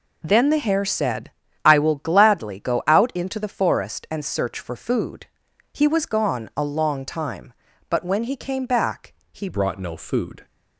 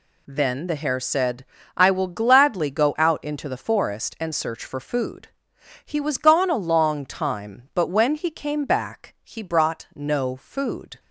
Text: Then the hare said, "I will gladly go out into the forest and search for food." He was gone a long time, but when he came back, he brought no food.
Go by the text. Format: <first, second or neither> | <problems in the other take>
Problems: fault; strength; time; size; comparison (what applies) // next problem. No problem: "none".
second | changes voice at "brought"; from 9.4 s on; 1.0 s long